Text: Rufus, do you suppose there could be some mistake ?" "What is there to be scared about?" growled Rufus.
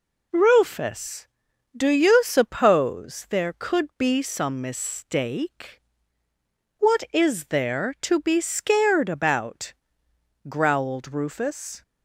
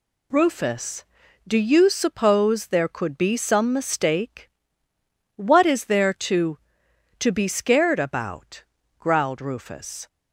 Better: first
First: none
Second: says "to" twice; at 7.1 s

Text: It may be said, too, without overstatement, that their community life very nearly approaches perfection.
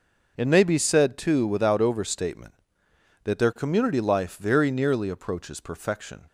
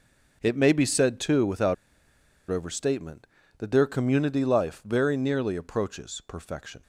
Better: first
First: none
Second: pauses between "without" and "overstatement"; noticeable; at 1.7 s; 0.75 s long

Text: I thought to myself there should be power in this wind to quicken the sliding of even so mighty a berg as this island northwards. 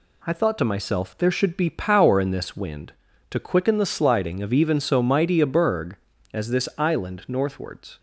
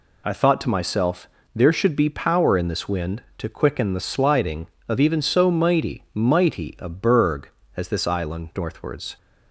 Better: first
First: none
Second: pauses between "myself" and "there"; slight; at 1.2 s; 0.26 s long // says "mighty" twice; at 6.1 s

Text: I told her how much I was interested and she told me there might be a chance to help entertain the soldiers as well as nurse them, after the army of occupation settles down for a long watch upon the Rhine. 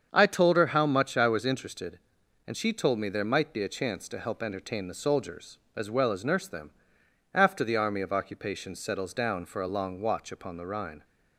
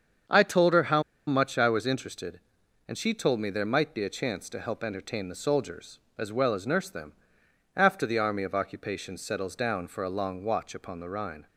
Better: first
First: starts louder than the rest; strong; until 1.1 s; 7 dB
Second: starts louder than the rest; strong; until 1.5 s; 7 dB // pauses between "how" and "much"; slight; at 1.0 s; 0.24 s long

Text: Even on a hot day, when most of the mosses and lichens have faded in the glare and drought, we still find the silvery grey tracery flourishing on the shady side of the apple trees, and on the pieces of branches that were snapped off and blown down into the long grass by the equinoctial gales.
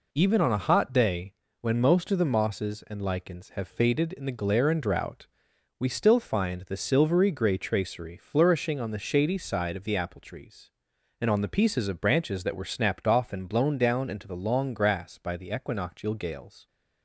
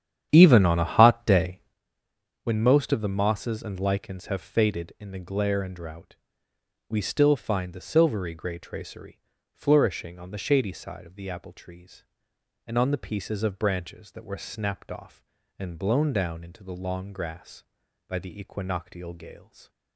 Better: first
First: none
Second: starts louder than the rest; strong; until 1.8 s; 9.5 dB // pauses between "tracery" and "flourishing"; slight; at 9.1 s; 0.34 s long

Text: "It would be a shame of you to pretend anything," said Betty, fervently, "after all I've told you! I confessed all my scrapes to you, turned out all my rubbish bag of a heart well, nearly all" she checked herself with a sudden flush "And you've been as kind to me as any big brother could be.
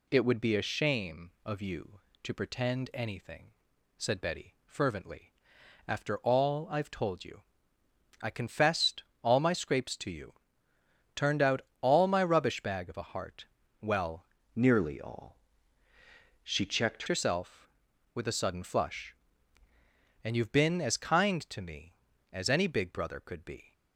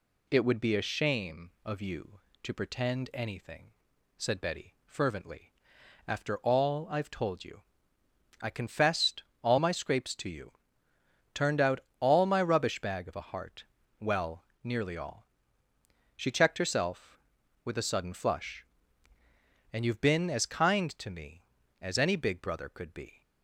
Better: second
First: pauses between "confessed" and "all"; slight; at 9.0 s; 0.18 s long // pauses between "out" and "all"; slight; at 11.5 s; 0.22 s long // pauses between "heart" and "well"; slight; at 13.4 s; 0.34 s long // changes voice from "nearly" to "checked"; from 14.5 to 17.0 s; 2.5 s long // pauses between "all" and "she"; at 15.3 s; 1.0 s long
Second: pauses between "confessed" and "all"; slight; at 9.2 s; 0.18 s long // pauses between "out" and "all"; slight; at 11.7 s; 0.22 s long // pauses between "heart" and "well"; slight; at 13.6 s; 0.34 s long // pauses between "all" and "she"; noticeable; at 15.2 s; 0.88 s long

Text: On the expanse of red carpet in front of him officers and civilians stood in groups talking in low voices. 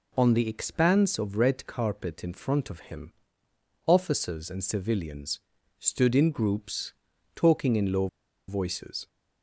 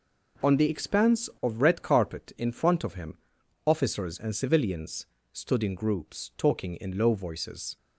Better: second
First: pauses between "him" and "officers"; noticeable; at 3.1 s; 0.74 s long // pauses between "civilians" and "stood"; at 5.4 s; 0.38 s long // pauses between "groups" and "talking"; at 6.9 s; 0.42 s long // pauses between "low" and "voices"; at 8.0 s; 0.41 s long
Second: pauses between "him" and "officers"; noticeable; at 3.1 s; 0.48 s long // pauses between "civilians" and "stood"; slight; at 5.0 s; 0.28 s long

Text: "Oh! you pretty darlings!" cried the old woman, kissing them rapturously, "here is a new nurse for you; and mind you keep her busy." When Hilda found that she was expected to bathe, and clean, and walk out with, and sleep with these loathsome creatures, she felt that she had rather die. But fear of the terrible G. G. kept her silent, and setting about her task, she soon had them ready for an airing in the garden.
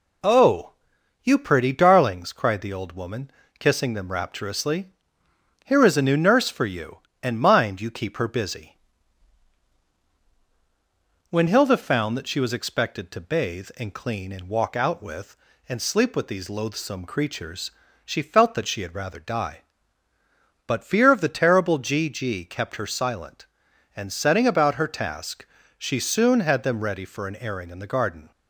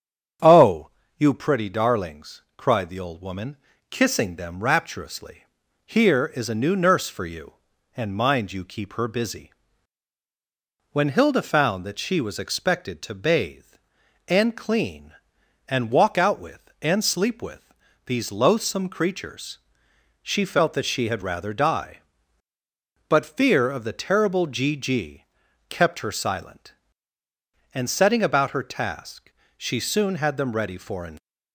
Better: first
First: none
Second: starts louder than the rest; strong; until 1.7 s; 8 dB // pauses between "with" and "these"; slight; at 17.7 s; 0.32 s long // pauses between "G" and "kept"; at 25.2 s; 0.44 s long // stops before "airing in the garden"; at 31.1 s

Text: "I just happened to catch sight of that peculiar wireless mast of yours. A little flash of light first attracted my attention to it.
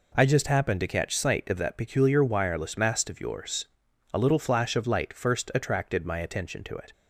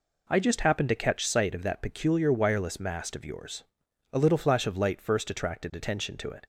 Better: first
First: none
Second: skips "my"; at 5.7 s

